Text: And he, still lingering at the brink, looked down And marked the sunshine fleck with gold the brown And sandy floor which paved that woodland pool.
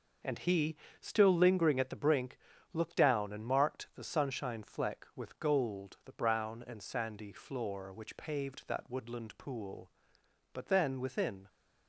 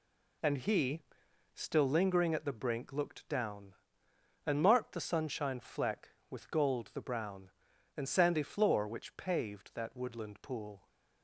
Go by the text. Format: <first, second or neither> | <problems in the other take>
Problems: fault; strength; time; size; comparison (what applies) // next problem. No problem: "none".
second | goes on to say "But then within"; noticeable; from 10.5 s on; 0.94 s long